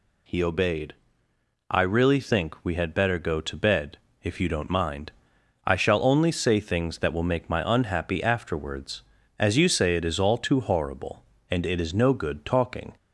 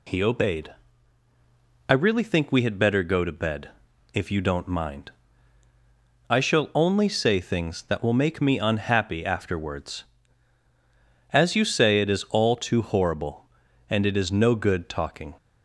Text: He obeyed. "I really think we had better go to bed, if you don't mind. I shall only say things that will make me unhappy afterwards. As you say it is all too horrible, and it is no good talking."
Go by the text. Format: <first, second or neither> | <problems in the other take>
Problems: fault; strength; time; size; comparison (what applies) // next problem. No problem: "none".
second | says "my" for "me"; at 7.4 s